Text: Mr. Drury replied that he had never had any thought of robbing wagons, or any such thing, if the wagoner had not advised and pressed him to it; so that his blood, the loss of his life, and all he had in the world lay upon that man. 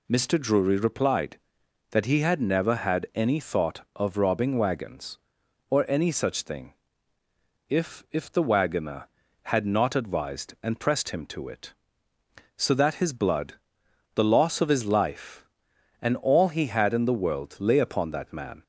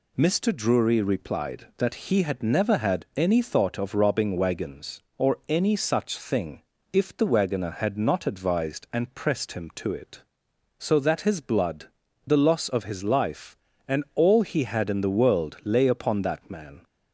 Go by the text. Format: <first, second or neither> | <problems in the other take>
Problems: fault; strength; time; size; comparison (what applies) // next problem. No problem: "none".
second | says "if" twice; at 8.1 s